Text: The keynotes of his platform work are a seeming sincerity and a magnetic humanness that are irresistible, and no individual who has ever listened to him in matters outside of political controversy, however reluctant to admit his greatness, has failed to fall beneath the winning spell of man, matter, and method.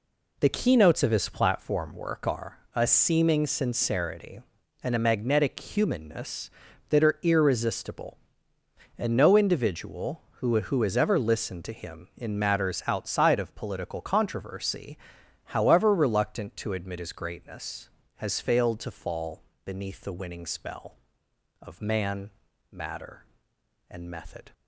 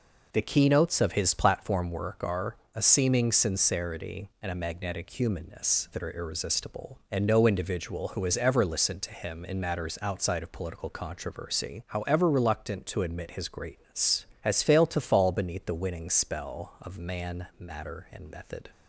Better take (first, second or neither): second